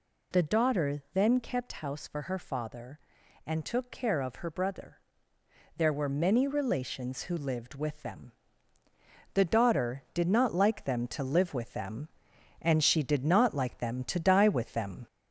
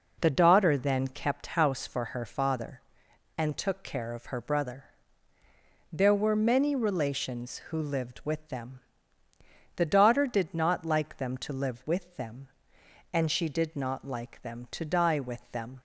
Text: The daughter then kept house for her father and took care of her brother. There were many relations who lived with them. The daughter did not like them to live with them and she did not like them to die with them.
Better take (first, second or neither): second